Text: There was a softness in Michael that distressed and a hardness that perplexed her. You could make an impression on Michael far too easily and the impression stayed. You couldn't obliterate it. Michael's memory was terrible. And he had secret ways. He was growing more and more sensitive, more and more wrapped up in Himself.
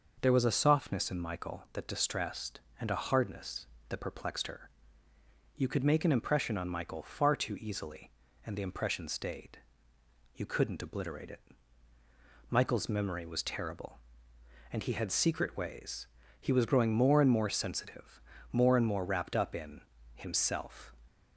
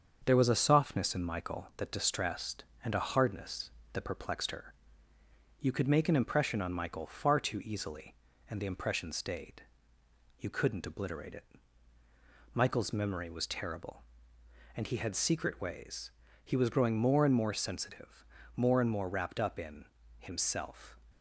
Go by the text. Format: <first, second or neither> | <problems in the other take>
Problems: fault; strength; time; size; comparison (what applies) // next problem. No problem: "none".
first | gets quieter; throughout; 3.5 dB // pauses between "in" and "Himself"; slight; at 19.8 s; 0.32 s long; slight in the first